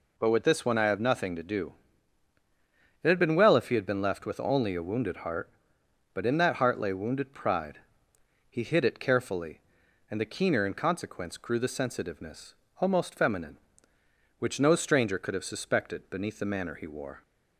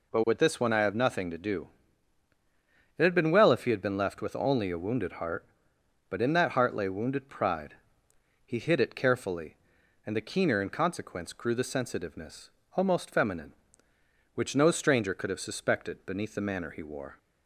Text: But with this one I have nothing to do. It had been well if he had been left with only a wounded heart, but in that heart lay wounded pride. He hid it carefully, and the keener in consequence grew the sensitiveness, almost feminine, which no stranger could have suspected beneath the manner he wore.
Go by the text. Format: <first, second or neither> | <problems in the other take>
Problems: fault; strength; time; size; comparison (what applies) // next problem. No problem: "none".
neither | none